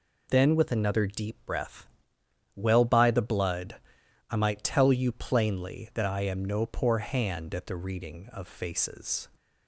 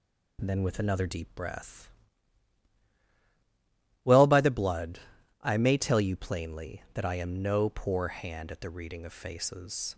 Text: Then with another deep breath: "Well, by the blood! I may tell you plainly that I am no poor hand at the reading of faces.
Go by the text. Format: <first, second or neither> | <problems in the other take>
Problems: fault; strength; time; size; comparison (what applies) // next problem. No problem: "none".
second | says "might" for "may"; at 4.3 s